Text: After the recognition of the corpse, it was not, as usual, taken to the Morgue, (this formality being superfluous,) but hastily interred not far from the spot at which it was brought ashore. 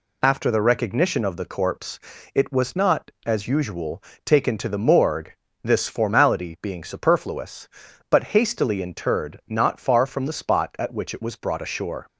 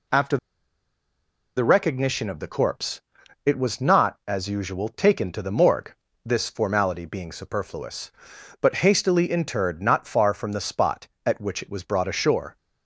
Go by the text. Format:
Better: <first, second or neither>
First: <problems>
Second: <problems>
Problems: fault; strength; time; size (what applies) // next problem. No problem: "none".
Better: first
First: none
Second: pauses between "After" and "the"; at 0.3 s; 1.1 s long